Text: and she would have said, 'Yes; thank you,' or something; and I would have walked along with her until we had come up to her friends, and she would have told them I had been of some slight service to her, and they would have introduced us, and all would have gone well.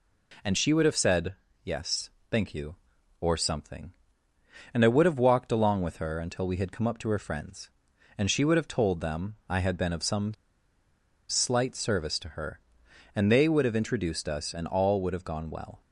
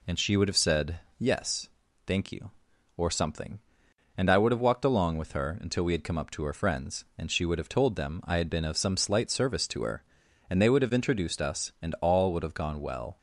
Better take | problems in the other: second | pauses between "some" and "slight"; noticeable; at 10.3 s; 0.94 s long

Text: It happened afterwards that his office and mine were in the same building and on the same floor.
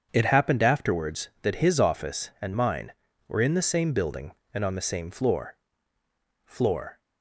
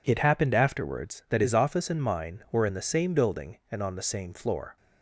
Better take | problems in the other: second | starts louder than the rest; strong; until 1.1 s; 7 dB // says "floor" twice; at 6.4 s

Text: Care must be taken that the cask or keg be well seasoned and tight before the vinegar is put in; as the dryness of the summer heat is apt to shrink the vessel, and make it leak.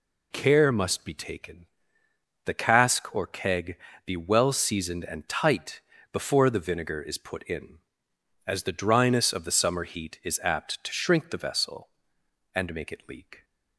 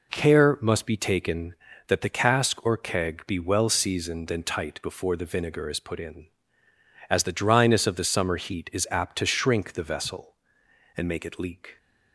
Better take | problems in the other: second | skips "that"; at 2.0 s // pauses between "keg" and "be"; slight; at 3.7 s; 0.30 s long // pauses between "tight" and "before"; slight; at 5.8 s; 0.30 s long

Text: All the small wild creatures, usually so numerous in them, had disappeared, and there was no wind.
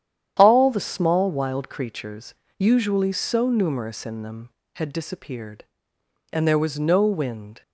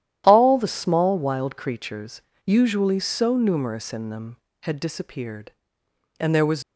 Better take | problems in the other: first | starts louder than the rest; strong; until 1.2 s; 11.5 dB; strong in the first // stops before "no wind"; at 6.6 s

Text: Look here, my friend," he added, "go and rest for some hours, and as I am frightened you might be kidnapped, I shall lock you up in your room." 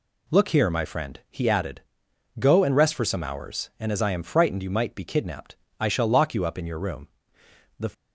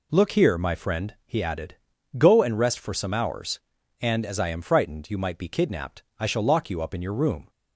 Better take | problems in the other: second | goes on to say "The"; slight; from 7.7 s on; 0.12 s long

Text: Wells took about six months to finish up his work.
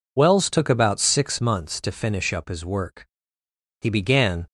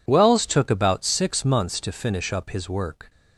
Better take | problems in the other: second | goes on to say "He began"; noticeable; from 3.8 s on; 0.66 s long

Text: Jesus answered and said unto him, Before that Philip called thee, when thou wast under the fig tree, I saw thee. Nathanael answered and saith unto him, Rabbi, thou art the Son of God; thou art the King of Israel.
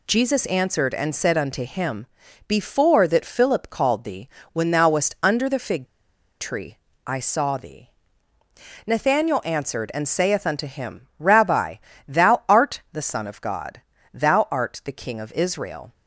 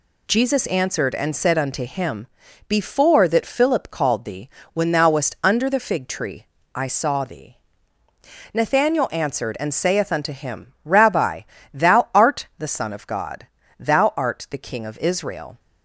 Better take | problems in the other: second | pauses between "fig" and "tree"; noticeable; at 5.8 s; 0.52 s long

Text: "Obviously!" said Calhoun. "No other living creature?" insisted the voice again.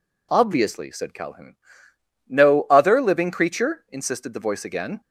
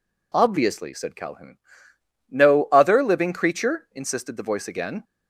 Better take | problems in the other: neither | none

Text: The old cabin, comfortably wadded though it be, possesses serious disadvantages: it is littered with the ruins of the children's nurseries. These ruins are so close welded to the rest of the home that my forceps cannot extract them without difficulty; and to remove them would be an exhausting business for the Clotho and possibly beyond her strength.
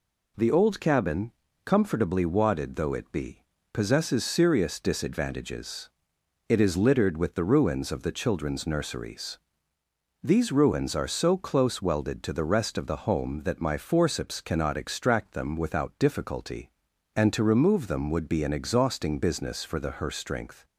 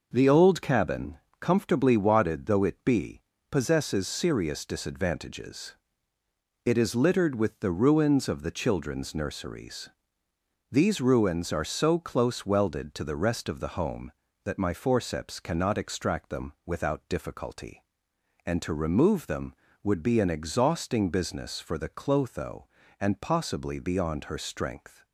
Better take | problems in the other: second | skips "Clotho and possibly beyond"; at 19.9 s

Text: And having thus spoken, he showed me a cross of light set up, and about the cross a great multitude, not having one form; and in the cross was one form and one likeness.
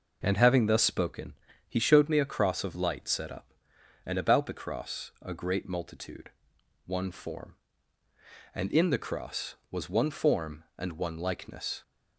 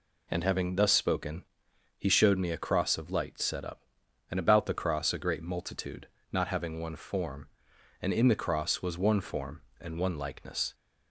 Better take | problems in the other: second | skips "not having"; at 6.5 s

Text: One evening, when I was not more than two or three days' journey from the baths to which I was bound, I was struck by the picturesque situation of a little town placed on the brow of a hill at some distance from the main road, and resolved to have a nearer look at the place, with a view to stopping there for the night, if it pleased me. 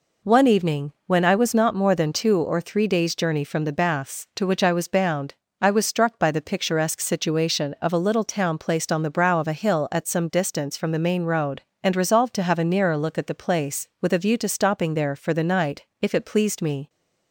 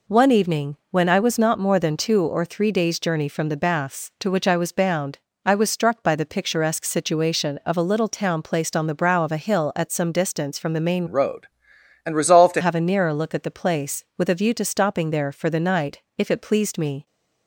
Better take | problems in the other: first | changes voice from "road" to "to"; from 11.0 to 12.6 s; 1.6 s long

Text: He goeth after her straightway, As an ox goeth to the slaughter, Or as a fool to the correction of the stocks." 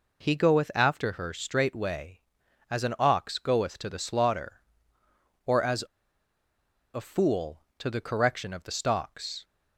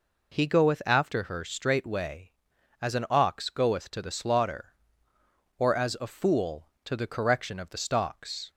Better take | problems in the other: second | pauses between "as" and "a"; at 5.8 s; 1.1 s long

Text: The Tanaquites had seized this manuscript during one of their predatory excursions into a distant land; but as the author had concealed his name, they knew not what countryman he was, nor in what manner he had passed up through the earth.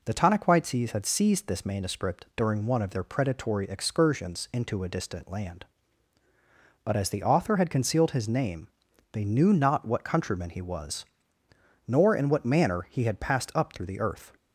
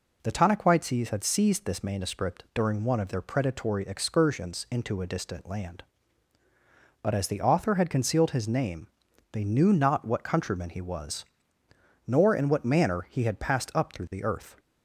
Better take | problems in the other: neither | none

